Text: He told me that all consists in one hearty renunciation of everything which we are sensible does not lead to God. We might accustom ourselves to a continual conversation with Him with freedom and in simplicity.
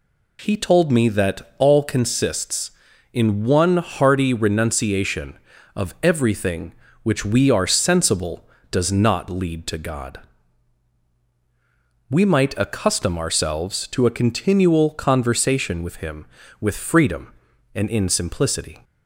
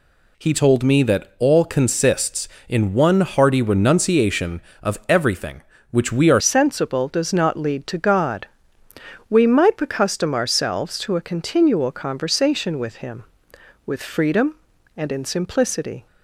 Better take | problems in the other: first | changes voice at "sensible"; from 6.4 s on; 9.6 s long

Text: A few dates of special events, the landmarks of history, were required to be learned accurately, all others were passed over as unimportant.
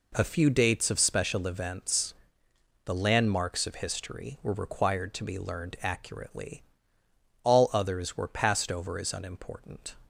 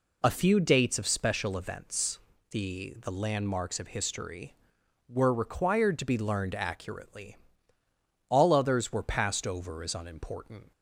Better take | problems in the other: first | says "the" twice; at 3.0 s

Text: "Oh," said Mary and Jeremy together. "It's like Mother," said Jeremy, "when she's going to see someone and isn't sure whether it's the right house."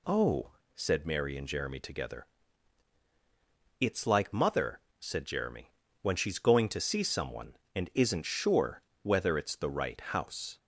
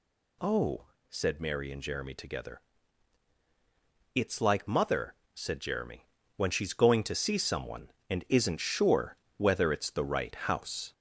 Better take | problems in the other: first | gets louder; slight; throughout; 3 dB // pauses between "sure" and "whether"; slight; at 9.1 s; 0.20 s long; slight in the first

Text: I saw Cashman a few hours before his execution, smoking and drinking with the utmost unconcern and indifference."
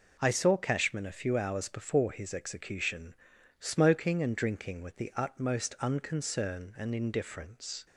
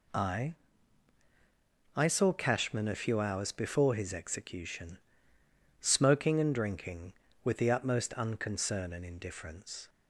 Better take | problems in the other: first | says "I" twice; at 1.9 s

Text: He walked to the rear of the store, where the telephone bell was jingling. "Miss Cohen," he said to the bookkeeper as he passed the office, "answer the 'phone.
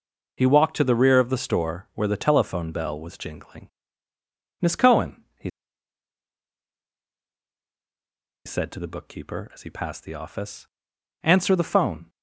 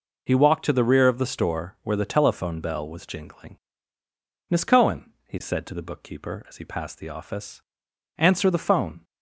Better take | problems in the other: second | pauses between "he" and "said"; strong; at 5.4 s; 2.9 s long

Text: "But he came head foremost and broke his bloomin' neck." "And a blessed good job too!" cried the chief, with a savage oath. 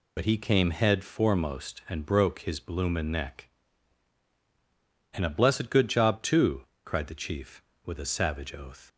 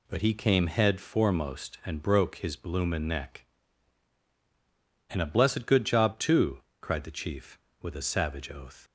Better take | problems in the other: second | loses the start of "But"; at 0.1 s; 60 ms

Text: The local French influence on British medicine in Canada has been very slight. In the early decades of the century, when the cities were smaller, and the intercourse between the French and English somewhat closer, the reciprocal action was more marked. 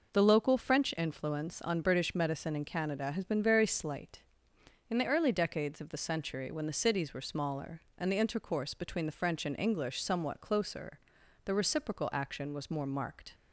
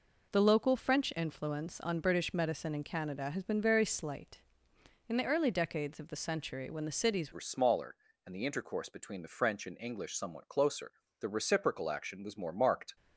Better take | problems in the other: first | changes voice at "were"; from 7.3 s on; 5.6 s long

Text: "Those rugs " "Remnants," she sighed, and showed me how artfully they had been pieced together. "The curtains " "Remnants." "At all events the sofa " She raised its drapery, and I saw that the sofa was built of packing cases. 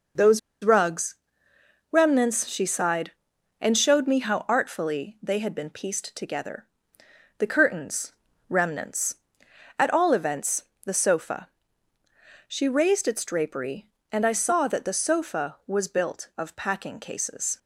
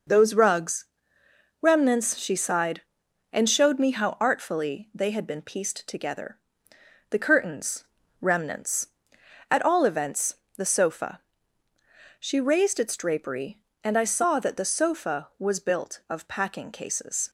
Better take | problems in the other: second | pauses between "Those" and "rugs"; slight; at 0.3 s; 0.24 s long // pauses between "events" and "the"; slight; at 10.6 s; 0.22 s long; slight in the second

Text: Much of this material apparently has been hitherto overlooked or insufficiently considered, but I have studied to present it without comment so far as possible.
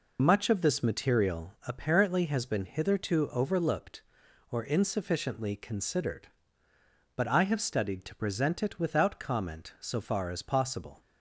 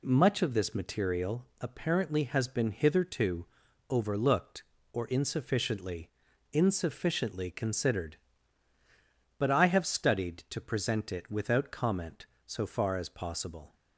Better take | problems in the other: first | pauses between "material" and "apparently"; slight; at 1.4 s; 0.16 s long // pauses between "hitherto" and "overlooked"; at 3.4 s; 0.44 s long // says "insufficiently" twice; at 6.5 s

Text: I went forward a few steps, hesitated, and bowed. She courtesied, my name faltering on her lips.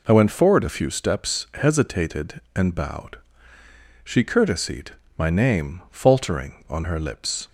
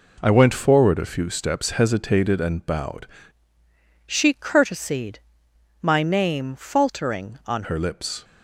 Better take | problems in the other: first | changes voice from "She" to "on"; from 4.0 to 7.6 s; 3.6 s long

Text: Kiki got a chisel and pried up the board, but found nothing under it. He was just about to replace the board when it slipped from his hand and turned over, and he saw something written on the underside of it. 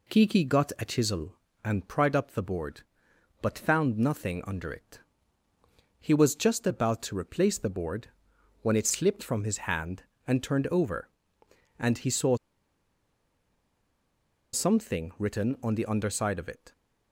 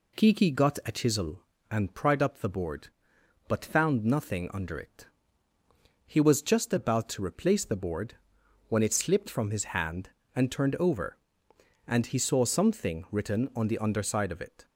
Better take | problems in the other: second | pauses between "board" and "when"; noticeable; at 8.0 s; 0.56 s long; noticeable in the second // pauses between "saw" and "something"; strong; at 12.3 s; 2.1 s long

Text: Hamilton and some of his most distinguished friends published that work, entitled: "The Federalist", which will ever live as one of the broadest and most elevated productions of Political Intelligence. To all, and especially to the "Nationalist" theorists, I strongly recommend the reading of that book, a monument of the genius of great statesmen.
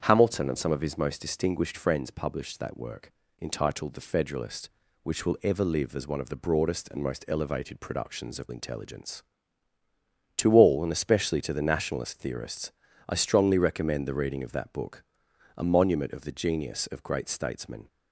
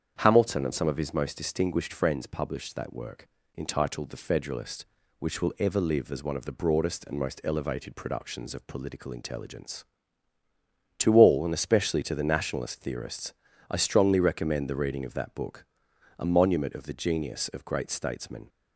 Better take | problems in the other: second | starts louder than the rest; strong; until 1.0 s; 8 dB; strong in the second // skips "Political"; at 8.5 s

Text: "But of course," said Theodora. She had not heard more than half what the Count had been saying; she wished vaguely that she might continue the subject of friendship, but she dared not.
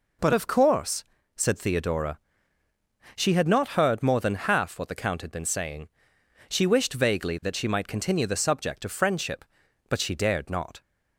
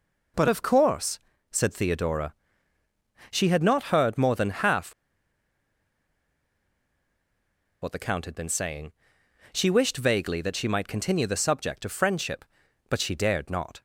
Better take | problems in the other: first | pauses between "half" and "what"; strong; at 4.9 s; 2.8 s long

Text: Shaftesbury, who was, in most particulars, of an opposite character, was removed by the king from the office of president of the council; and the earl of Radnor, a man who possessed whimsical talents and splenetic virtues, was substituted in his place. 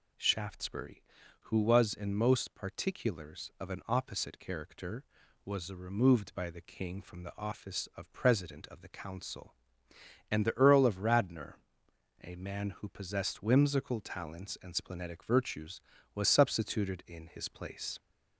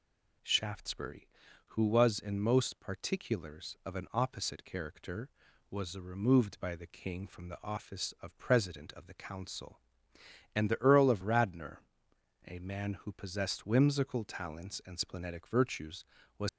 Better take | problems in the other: first | stops before "substituted in his place"; at 16.4 s

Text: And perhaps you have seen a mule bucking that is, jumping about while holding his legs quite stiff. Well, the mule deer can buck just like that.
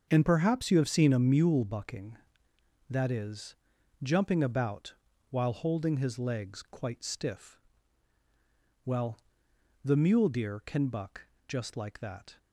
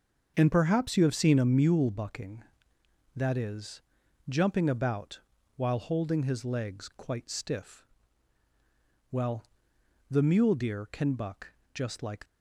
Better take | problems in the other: first | starts louder than the rest; until 1.3 s; 6.5 dB; also in the first // pauses between "about" and "while"; slight; at 5.1 s; 0.36 s long; slight in the first // pauses between "buck" and "just"; slight; at 11.5 s; 0.20 s long; slight in the first // stops before "that"; at 12.2 s

